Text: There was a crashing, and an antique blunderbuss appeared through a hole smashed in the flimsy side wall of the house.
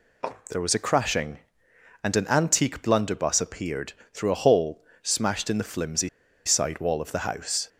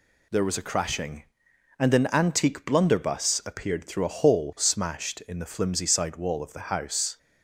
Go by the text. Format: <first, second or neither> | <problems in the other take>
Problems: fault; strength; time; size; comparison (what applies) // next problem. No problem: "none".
second | pauses between "appeared" and "through"; slight; at 3.9 s; 0.20 s long // pauses between "hole" and "smashed"; slight; at 4.8 s; 0.18 s long // pauses between "flimsy" and "side"; at 6.0 s; 0.37 s long